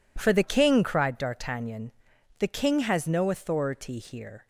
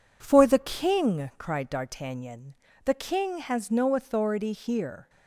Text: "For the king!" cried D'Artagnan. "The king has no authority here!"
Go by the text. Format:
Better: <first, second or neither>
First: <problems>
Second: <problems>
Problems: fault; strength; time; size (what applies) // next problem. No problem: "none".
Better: neither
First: none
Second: none